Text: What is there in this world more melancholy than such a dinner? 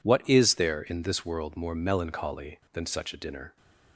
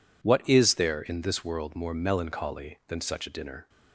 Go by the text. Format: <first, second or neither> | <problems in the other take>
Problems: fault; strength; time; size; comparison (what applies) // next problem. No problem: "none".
neither | none